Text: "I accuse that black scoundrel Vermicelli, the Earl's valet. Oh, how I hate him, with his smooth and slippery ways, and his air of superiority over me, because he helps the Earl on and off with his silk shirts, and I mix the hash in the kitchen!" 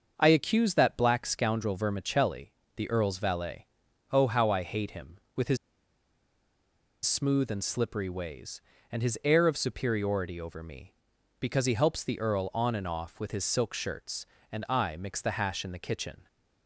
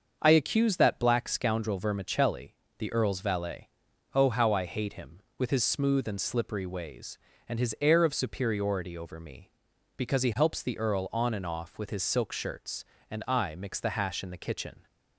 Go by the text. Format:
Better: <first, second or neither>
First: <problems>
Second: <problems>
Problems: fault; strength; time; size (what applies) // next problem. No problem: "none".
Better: second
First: starts louder than the rest; until 1.1 s; 6.5 dB // pauses between "his" and "smooth"; strong; at 5.5 s; 1.4 s long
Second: starts louder than the rest; until 1.2 s; 6.5 dB